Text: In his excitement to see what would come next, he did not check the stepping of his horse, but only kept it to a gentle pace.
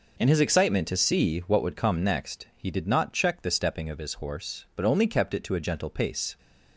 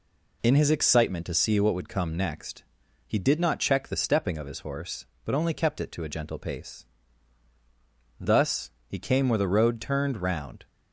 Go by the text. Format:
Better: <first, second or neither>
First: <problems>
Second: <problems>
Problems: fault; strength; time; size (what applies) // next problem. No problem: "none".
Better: first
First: none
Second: goes on to say "Thus he came where the road turned round"; strong; from 8.1 s on; 2.4 s long